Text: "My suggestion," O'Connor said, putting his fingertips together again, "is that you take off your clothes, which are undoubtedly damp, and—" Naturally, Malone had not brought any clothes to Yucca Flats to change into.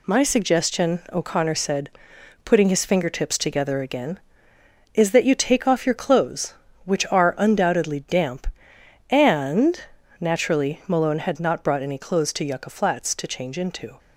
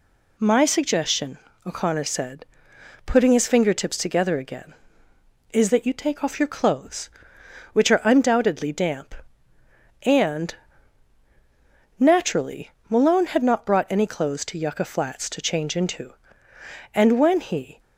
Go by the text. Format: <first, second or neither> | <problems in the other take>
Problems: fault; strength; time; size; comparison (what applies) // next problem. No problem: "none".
first | goes on to say "And when he"; noticeable; from 16.9 s on; 0.84 s long